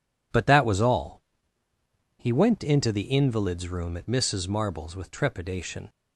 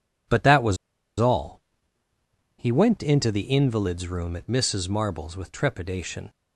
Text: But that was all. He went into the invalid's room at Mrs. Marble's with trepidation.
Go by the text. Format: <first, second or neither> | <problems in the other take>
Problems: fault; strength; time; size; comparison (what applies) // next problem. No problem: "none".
first | pauses between "was" and "all"; at 0.7 s; 0.43 s long